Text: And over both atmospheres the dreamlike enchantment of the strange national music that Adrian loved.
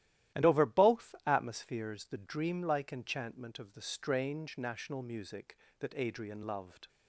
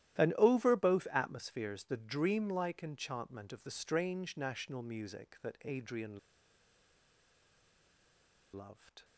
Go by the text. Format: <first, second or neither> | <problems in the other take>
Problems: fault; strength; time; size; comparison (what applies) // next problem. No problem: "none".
first | starts louder than the rest; strong; until 1.2 s; 13 dB; strong in the first // pauses between "Adrian" and "loved"; strong; at 6.1 s; 2.3 s long